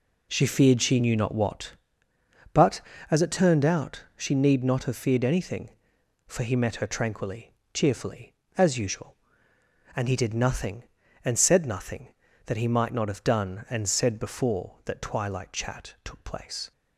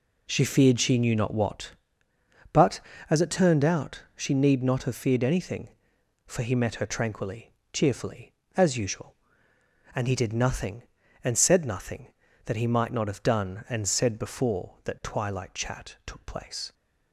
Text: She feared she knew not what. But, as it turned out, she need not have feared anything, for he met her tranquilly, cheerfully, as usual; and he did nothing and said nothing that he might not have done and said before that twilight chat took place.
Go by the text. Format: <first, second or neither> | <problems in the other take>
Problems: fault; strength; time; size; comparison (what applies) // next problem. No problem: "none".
neither | none